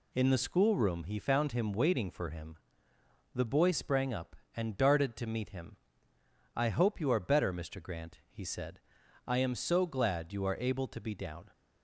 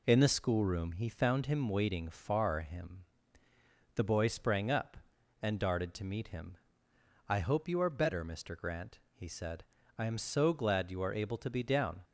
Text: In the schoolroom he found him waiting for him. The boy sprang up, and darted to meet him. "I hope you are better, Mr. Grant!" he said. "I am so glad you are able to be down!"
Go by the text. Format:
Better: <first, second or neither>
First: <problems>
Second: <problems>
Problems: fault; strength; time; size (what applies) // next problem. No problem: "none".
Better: first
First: none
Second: says "far" for "for"; at 2.0 s